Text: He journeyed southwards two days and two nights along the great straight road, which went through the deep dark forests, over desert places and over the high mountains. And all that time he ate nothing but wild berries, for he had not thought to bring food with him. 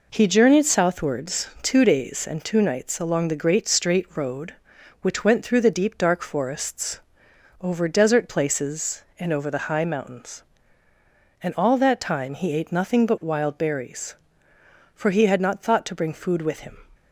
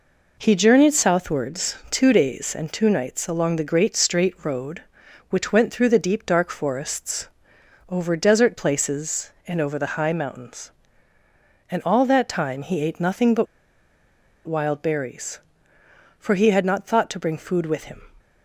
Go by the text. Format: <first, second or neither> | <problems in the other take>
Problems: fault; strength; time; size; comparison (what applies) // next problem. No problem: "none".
first | pauses between "but" and "wild"; at 13.4 s; 1.0 s long